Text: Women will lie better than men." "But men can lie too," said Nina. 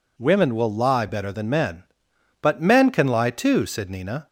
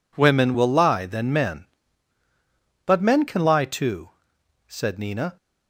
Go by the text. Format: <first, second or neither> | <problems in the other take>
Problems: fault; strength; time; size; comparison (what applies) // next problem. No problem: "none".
first | skips "better"; at 1.0 s